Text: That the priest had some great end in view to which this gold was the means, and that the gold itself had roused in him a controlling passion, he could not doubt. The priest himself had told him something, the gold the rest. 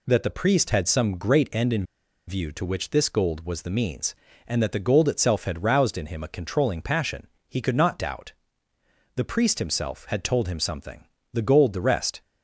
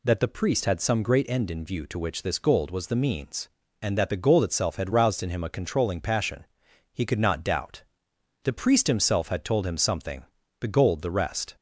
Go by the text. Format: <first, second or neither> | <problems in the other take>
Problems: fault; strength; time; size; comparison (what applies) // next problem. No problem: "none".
second | pauses between "in" and "view"; at 1.8 s; 0.44 s long